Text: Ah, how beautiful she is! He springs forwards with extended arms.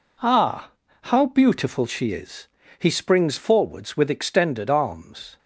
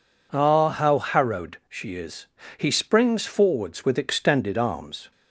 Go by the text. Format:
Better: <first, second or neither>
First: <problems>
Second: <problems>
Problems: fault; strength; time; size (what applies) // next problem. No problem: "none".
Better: first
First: none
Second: says "harrowed" for "beautiful"; at 0.9 s